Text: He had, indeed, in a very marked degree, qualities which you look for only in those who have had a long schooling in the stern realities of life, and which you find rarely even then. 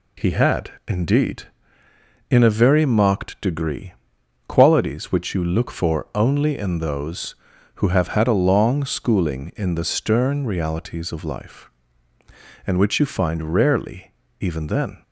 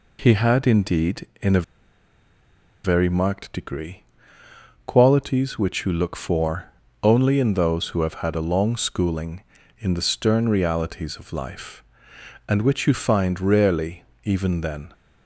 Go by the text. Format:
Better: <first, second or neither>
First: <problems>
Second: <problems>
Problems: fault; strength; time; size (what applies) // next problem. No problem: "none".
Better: first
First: pauses between "rarely" and "even"; slight; at 14.1 s; 0.28 s long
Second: pauses between "a" and "very"; at 1.6 s; 1.2 s long // pauses between "for" and "only"; slight; at 6.6 s; 0.36 s long // pauses between "rarely" and "even"; slight; at 14.0 s; 0.18 s long